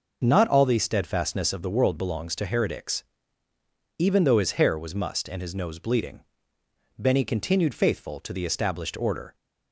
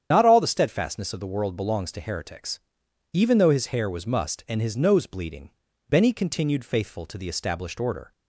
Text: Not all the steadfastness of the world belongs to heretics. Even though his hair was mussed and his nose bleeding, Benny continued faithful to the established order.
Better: first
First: none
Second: loses the start of "Not"; at 0.1 s; 70 ms // starts louder than the rest; strong; until 1.1 s; 9 dB

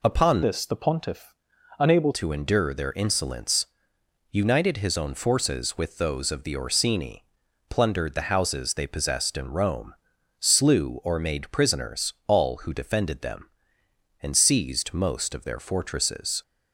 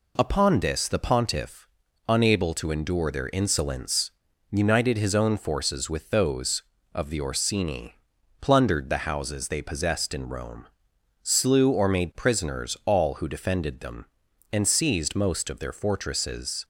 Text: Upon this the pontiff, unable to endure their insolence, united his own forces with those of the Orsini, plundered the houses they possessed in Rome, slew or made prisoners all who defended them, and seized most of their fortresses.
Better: second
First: changes voice from "this" to "unable"; from 0.4 to 2.1 s; 1.7 s long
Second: none

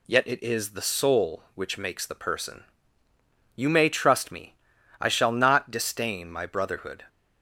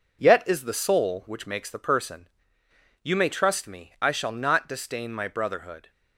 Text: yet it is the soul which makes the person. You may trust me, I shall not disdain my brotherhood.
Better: first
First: none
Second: skips "it"; at 0.4 s

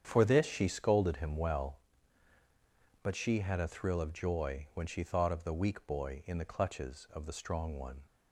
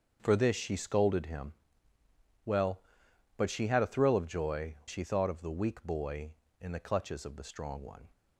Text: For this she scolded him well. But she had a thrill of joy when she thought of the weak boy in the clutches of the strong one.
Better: first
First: starts louder than the rest; strong; until 1.0 s; 8 dB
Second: starts louder than the rest; until 1.2 s; 6.5 dB // pauses between "him" and "well"; noticeable; at 1.5 s; 0.92 s long // skips "when"; at 4.8 s

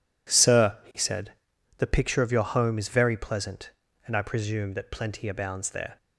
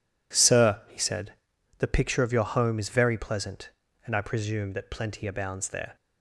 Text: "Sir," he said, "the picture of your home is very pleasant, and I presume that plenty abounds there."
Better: neither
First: none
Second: none

